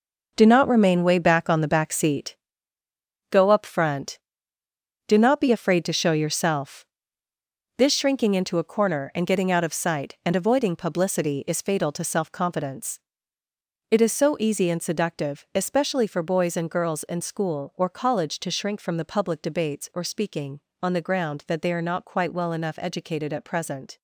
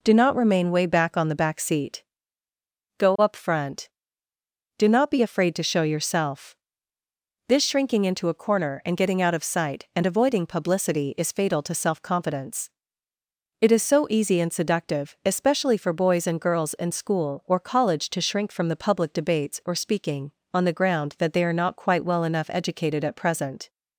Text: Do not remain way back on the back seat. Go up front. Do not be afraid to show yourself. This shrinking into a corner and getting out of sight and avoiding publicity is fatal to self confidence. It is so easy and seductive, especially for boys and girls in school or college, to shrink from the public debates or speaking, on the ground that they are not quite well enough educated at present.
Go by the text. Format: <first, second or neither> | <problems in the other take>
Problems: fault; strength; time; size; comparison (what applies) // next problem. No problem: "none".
second | gets quieter; strong; throughout; 9.5 dB